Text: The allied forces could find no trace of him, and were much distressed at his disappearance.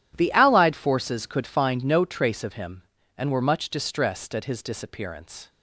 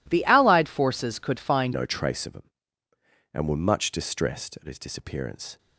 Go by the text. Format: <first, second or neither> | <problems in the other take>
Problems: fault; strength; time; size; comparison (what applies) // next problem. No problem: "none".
first | changes voice at "no"; from 1.7 s on; 3.8 s long